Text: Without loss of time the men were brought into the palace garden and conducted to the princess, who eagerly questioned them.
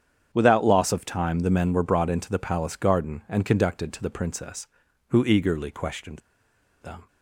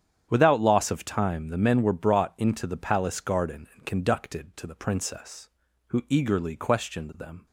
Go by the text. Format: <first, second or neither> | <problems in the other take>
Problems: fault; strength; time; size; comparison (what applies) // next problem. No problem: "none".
second | starts louder than the rest; strong; until 1.3 s; 8.5 dB; strong in the second // pauses between "questioned" and "them"; noticeable; at 6.1 s; 0.63 s long